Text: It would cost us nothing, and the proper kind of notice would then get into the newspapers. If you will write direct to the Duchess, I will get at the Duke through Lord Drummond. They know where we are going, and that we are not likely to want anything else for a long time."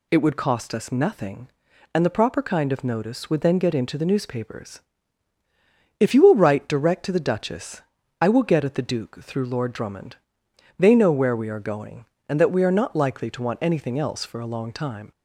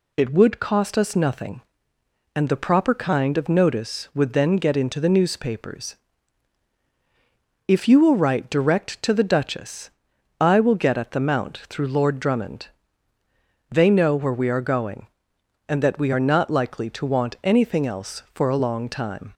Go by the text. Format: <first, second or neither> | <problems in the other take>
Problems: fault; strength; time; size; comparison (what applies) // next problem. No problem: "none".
first | says "Mount" for "Duke"; at 11.1 s